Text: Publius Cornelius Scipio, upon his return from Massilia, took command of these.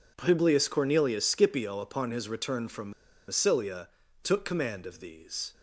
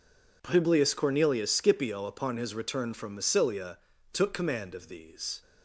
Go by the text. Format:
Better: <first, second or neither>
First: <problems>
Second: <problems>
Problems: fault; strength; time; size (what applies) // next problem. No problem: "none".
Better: second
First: pauses between "from" and "Massilia"; at 2.9 s; 0.36 s long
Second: none